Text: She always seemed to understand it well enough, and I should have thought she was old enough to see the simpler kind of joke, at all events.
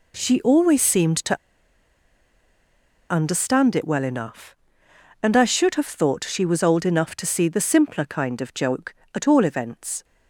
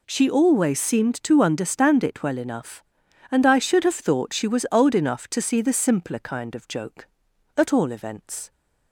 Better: second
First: pauses between "to" and "understand"; strong; at 1.3 s; 1.7 s long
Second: none

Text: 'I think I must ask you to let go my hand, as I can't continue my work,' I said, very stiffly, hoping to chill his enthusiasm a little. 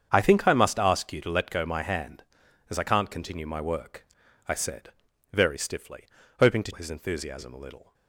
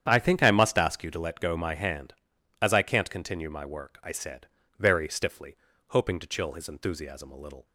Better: second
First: starts louder than the rest; strong; until 1.1 s; 7.5 dB // skips "chill"; at 6.7 s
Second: starts louder than the rest; strong; until 1.0 s; 9 dB

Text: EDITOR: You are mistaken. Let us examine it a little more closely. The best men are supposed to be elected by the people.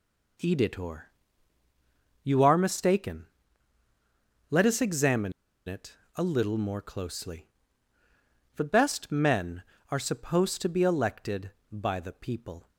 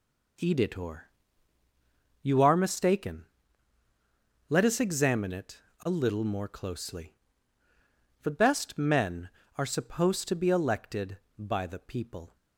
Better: second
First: pauses between "examine" and "it"; slight; at 5.3 s; 0.34 s long // pauses between "it" and "a"; slight; at 5.9 s; 0.20 s long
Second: pauses between "it" and "a"; slight; at 5.5 s; 0.20 s long

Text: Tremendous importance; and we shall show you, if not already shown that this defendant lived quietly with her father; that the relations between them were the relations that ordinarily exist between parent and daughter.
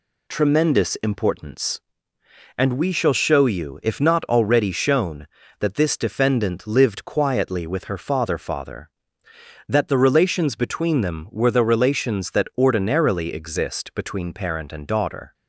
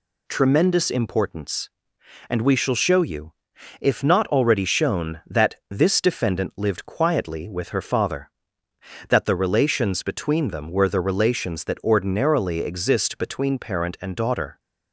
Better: second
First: says "father" twice; at 8.3 s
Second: none

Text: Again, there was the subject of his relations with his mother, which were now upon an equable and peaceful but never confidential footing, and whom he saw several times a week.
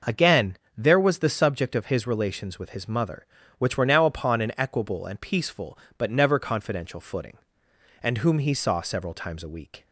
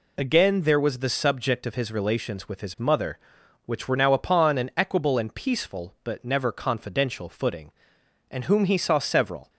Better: first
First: none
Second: stops before "times a week"; at 9.4 s

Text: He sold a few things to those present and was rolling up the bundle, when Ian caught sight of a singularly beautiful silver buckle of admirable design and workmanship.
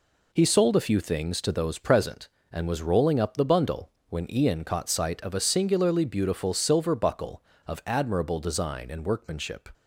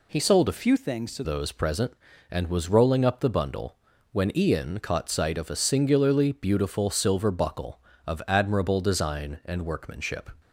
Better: first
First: none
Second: changes voice from "few" to "to"; from 0.5 to 1.2 s; 0.7 s long

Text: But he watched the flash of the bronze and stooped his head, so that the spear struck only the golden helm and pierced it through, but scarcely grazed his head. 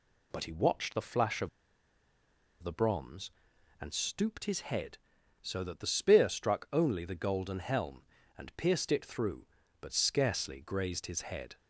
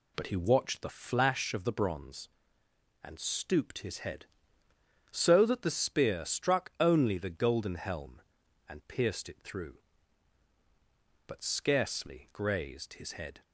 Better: second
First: pauses between "of" and "the"; at 1.4 s; 1.1 s long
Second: none

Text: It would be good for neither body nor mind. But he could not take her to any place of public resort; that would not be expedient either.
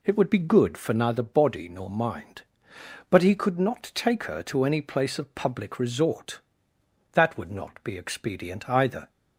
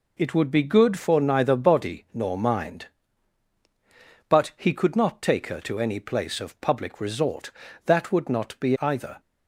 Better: first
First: none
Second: skips "expedient"; at 8.7 s

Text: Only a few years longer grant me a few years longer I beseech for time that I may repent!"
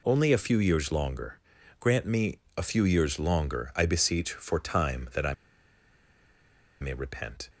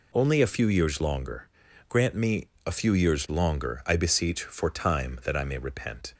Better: second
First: pauses between "longer" and "grant"; at 1.3 s; 0.42 s long // pauses between "me" and "a"; slight; at 2.3 s; 0.18 s long // pauses between "I" and "may"; strong; at 5.3 s; 1.4 s long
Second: pauses between "longer" and "grant"; at 1.4 s; 0.42 s long // pauses between "me" and "a"; slight; at 2.4 s; 0.18 s long

